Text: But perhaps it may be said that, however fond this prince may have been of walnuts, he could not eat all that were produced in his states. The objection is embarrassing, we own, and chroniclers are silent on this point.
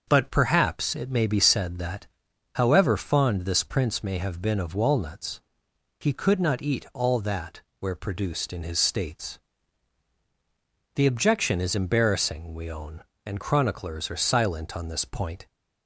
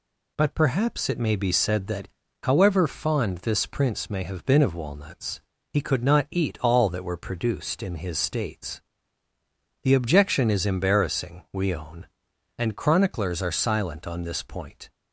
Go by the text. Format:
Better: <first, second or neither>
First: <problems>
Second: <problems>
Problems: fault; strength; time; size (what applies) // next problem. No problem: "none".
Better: second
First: starts louder than the rest; until 1.0 s; 6.5 dB // says "where" for "were"; at 7.7 s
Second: none